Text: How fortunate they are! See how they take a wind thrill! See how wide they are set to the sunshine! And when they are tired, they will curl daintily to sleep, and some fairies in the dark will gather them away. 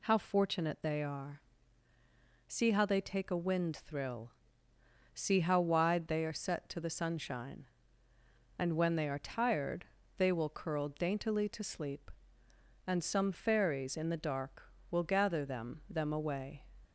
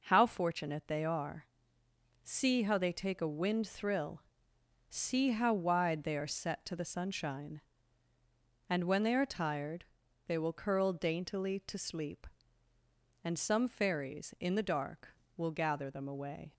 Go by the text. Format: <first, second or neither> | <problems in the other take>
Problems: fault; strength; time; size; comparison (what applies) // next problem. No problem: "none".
second | says "them" twice; at 15.8 s